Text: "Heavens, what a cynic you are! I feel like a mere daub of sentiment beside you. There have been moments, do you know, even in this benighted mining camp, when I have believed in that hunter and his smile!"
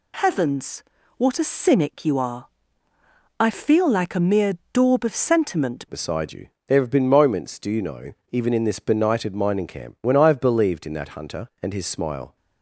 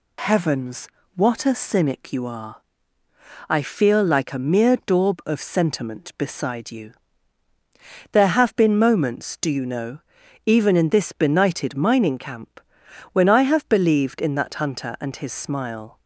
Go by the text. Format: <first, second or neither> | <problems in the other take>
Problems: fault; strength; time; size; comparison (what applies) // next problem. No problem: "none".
second | pauses between "mere" and "daub"; slight; at 4.5 s; 0.18 s long // changes voice at "beside"; from 5.8 s on; 6.5 s long